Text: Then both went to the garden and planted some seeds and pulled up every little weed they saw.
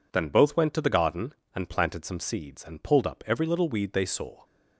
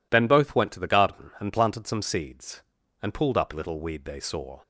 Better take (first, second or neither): first